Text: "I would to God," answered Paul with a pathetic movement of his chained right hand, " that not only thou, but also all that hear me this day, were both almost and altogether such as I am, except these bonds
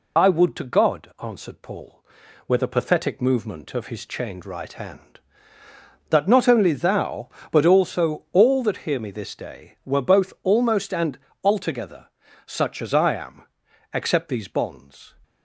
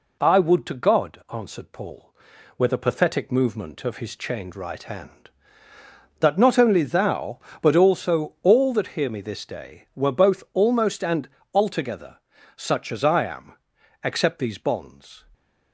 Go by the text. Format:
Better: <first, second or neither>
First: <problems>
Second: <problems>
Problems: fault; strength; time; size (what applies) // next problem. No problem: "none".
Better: second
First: loses the start of "I"; at 0.1 s; 65 ms // pauses between "and" and "altogether"; slight; at 11.1 s; 0.26 s long // pauses between "altogether" and "such"; slight; at 12.0 s; 0.36 s long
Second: pauses between "and" and "altogether"; slight; at 11.2 s; 0.26 s long // pauses between "altogether" and "such"; slight; at 12.1 s; 0.36 s long